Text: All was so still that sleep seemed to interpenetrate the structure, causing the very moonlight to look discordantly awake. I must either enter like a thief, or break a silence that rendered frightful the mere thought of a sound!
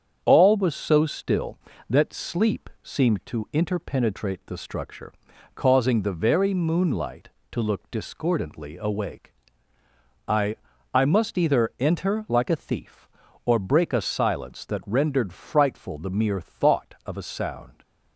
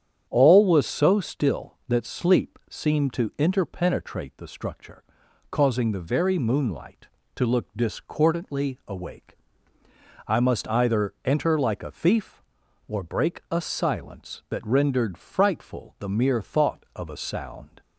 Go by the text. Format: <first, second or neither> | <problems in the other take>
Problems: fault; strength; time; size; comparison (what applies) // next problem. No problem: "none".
second | starts louder than the rest; strong; until 1.2 s; 7.5 dB; strong in the second // says "I" twice; at 10.9 s